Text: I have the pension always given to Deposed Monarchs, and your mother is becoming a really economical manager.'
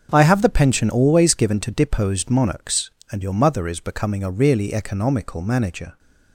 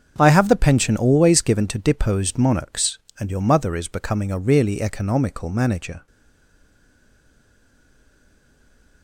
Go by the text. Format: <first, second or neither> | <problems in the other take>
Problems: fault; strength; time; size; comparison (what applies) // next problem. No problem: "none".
first | starts louder than the rest; strong; until 1.2 s; 7 dB; also in the first // stays silent after the last word; strong; from 6.0 s on; 3.0 s long